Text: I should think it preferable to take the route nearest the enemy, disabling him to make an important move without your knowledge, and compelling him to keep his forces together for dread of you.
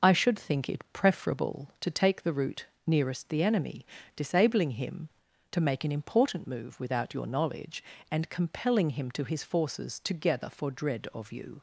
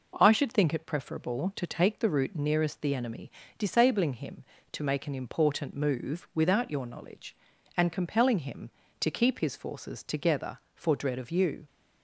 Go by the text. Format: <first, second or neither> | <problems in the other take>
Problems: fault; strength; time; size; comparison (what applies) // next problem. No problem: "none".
second | pauses between "route" and "nearest"; slight; at 2.6 s; 0.22 s long // skips "keep"; at 9.2 s